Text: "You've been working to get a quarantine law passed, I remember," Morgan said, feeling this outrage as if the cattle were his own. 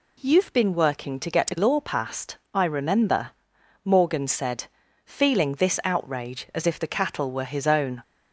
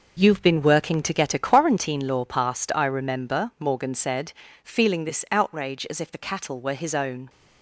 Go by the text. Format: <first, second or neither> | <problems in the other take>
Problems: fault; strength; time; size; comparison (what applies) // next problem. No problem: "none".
second | skips "quarantine"; at 1.5 s